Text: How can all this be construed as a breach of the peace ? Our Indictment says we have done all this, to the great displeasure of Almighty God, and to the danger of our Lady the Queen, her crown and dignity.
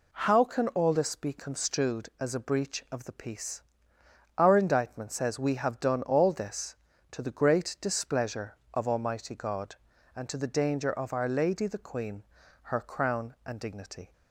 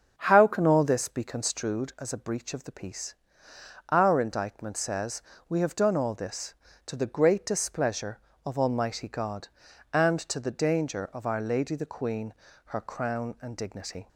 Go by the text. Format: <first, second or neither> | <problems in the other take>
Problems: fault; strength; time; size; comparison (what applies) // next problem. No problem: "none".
first | starts louder than the rest; until 1.8 s; 7 dB // pauses between "says" and "we"; slight; at 5.2 s; 0.26 s long